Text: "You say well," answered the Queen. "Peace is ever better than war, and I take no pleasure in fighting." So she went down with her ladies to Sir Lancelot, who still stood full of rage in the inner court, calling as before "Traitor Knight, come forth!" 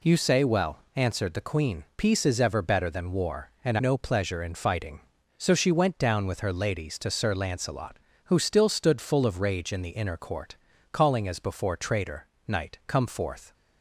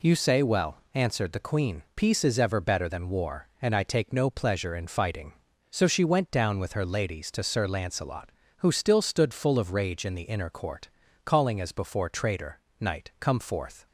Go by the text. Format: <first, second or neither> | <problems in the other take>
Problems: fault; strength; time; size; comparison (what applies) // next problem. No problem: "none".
second | skips "I take"; at 3.7 s // pauses between "Traitor" and "Knight"; slight; at 12.2 s; 0.20 s long; slight in the second